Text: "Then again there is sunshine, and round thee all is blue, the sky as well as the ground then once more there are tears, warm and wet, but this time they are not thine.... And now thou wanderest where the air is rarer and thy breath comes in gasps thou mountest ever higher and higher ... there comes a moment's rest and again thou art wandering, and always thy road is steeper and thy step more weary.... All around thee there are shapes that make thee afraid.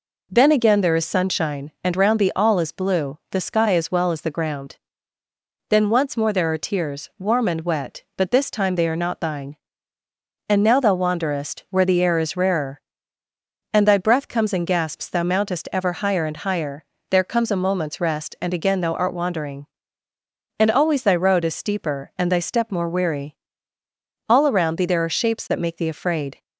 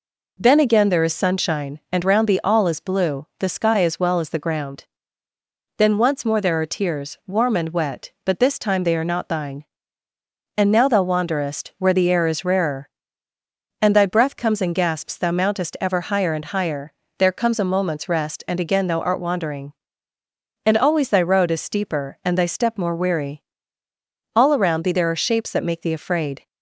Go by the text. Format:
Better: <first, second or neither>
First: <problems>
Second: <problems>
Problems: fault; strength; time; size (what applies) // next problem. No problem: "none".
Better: neither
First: pauses between "ground" and "then"; noticeable; at 4.7 s; 0.94 s long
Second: pauses between "ground" and "then"; noticeable; at 4.8 s; 0.94 s long